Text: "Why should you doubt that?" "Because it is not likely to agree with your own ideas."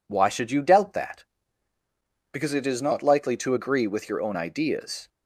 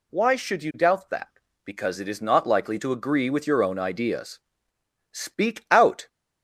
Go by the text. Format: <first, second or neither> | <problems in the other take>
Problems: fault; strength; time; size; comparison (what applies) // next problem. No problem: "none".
first | goes on to say "Speak out"; noticeable; from 5.0 s on; 0.98 s long